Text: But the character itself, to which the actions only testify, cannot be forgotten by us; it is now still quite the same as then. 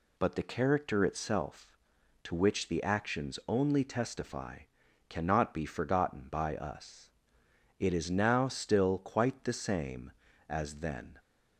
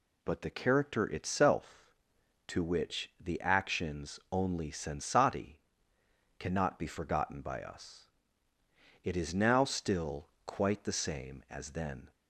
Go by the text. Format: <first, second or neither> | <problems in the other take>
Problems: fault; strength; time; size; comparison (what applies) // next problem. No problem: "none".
first | says "sensati" for "testify"; at 4.7 s // pauses between "still" and "quite"; slight; at 10.2 s; 0.16 s long